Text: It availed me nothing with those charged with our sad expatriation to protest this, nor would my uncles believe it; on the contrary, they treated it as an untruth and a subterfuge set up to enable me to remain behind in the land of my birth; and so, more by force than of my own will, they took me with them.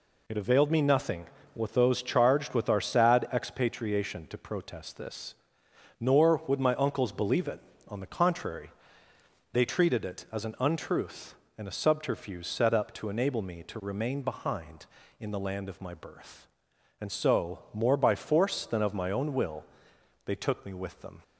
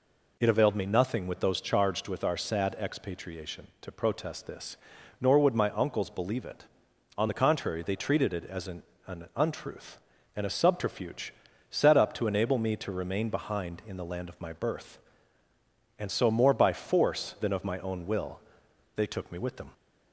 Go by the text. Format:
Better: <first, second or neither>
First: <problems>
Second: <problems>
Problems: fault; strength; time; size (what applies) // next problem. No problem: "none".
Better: first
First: none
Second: says "an" twice; at 9.0 s // pauses between "subterfuge" and "set"; at 11.3 s; 0.38 s long